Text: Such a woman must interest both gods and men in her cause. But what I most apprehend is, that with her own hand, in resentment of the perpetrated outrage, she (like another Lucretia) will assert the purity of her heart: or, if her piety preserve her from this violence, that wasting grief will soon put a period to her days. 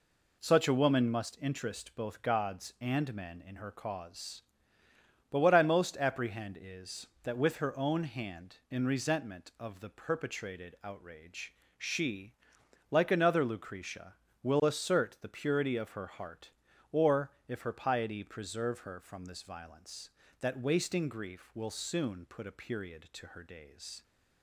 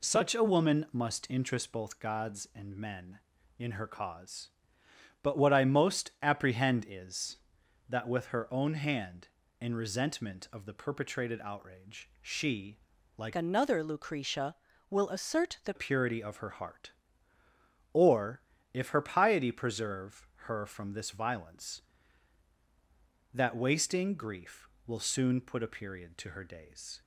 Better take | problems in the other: first | changes voice from "another" to "the"; from 13.3 to 15.7 s; 2.4 s long // pauses between "preserve" and "her"; slight; at 20.2 s; 0.18 s long

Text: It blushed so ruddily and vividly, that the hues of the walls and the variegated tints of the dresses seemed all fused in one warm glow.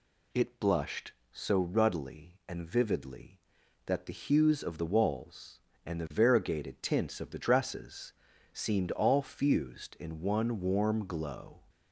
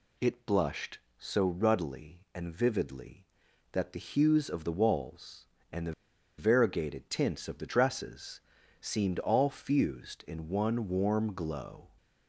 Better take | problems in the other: first | pauses between "the" and "variegated"; noticeable; at 5.9 s; 0.46 s long // pauses between "dresses" and "seemed"; at 8.3 s; 0.40 s long; also in the first

